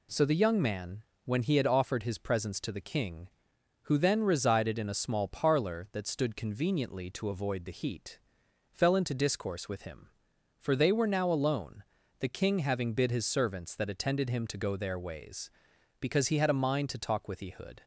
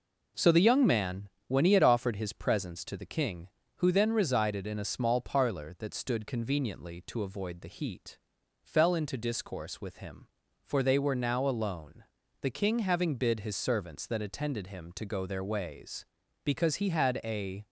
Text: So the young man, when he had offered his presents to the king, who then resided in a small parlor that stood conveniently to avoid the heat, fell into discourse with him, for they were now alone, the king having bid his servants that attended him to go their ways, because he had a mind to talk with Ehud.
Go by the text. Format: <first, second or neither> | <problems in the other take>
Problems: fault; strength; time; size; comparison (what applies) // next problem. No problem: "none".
first | stops before "mind to talk with Ehud"; at 17.6 s